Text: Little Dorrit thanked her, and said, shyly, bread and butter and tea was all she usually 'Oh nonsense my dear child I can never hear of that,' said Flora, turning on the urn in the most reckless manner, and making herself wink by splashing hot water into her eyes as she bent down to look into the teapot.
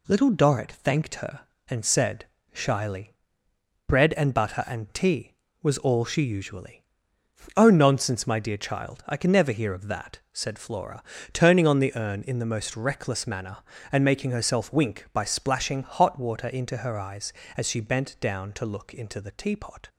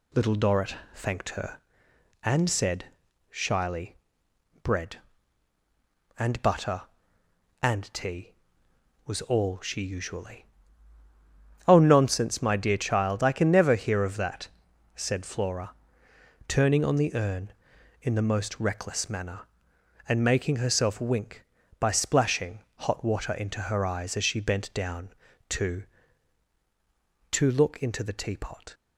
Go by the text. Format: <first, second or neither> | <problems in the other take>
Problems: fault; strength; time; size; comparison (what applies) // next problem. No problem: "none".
first | pauses between "Dorrit" and "thanked"; slight; at 0.7 s; 0.20 s long // pauses between "usually" and "Oh"; at 10.4 s; 1.2 s long; noticeable in the first // pauses between "splashing" and "hot"; slight; at 22.5 s; 0.18 s long // says "to" twice; at 27.2 s